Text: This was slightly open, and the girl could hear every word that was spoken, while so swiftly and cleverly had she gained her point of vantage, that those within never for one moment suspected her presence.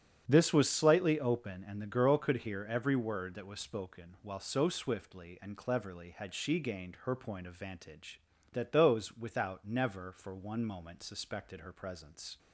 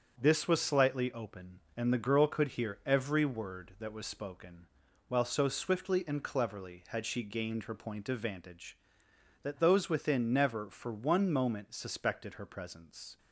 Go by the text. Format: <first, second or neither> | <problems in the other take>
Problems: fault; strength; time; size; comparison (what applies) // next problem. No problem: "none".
second | starts louder than the rest; strong; until 1.2 s; 8 dB // says "without" for "within"; at 9.1 s